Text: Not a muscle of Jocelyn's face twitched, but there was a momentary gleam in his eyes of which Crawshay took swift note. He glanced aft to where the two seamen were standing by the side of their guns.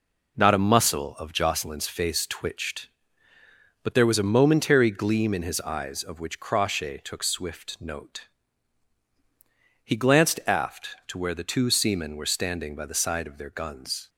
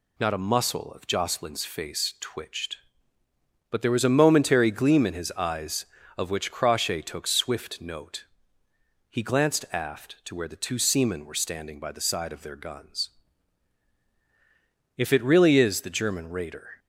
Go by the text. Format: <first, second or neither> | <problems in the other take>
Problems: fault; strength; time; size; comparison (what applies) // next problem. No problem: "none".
first | goes on to say "If it really is the German raider"; strong; from 14.9 s on; 1.8 s long